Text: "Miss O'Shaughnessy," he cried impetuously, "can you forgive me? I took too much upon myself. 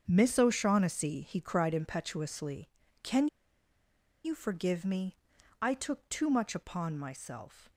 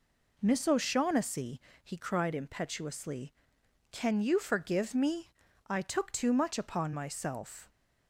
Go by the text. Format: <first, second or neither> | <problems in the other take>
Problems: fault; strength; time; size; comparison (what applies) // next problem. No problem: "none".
second | starts louder than the rest; strong; until 1.0 s; 7 dB // pauses between "can" and "you"; at 3.2 s; 0.98 s long